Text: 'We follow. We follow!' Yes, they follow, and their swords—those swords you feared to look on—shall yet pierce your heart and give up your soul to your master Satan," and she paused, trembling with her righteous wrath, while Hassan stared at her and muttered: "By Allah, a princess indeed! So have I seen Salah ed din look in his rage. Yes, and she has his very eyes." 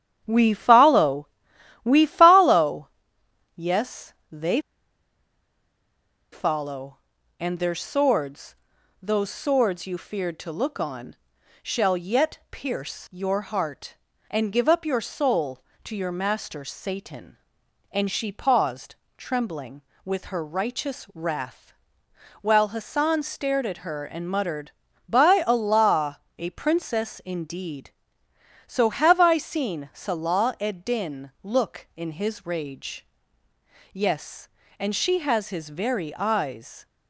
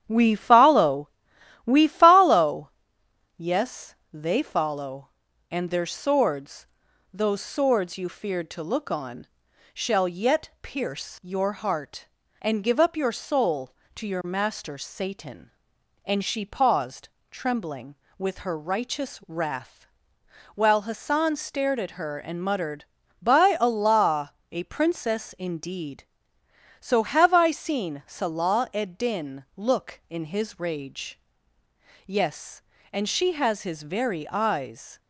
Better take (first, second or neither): second